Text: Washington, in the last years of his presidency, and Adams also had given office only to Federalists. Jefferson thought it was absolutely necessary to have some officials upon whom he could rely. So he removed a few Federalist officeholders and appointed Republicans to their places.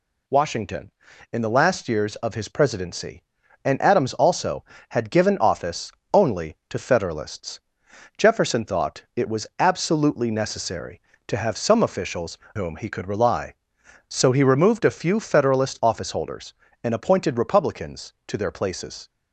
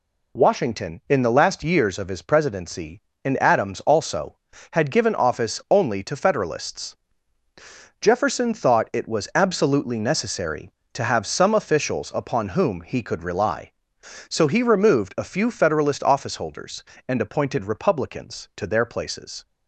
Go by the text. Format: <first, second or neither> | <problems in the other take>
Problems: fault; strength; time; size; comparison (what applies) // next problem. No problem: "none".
second | pauses between "office" and "only"; slight; at 5.9 s; 0.20 s long // skips "upon"; at 12.4 s